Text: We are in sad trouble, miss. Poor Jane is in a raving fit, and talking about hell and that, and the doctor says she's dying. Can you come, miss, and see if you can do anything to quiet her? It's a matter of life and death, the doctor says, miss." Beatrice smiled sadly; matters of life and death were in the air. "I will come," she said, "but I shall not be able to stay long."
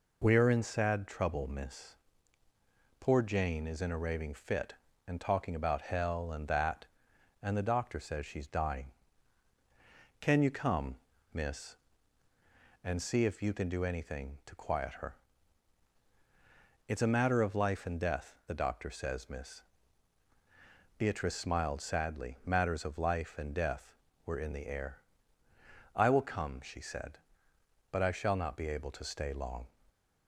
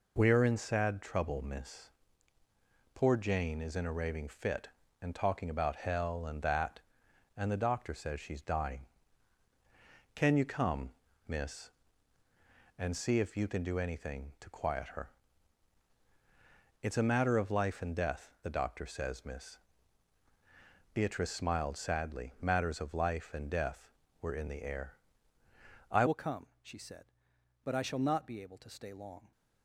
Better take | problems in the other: first | changes voice at "will"; from 26.0 s on; 3.3 s long

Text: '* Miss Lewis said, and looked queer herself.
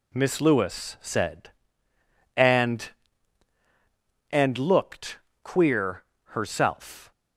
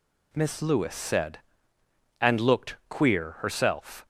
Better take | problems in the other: second | says "and" twice; at 4.3 s // pauses between "looked" and "queer"; slight; at 5.1 s; 0.26 s long // pauses between "queer" and "herself"; slight; at 6.0 s; 0.22 s long

